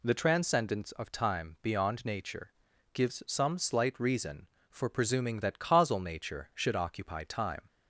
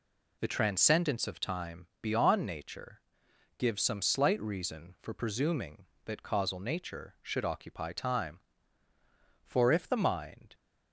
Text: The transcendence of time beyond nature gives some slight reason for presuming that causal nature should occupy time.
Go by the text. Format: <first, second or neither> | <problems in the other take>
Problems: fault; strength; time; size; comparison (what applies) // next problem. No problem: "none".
first | pauses between "nature" and "gives"; noticeable; at 2.9 s; 0.58 s long; also in the first // goes on to say "For if the mind"; noticeable; from 9.4 s on; 1.1 s long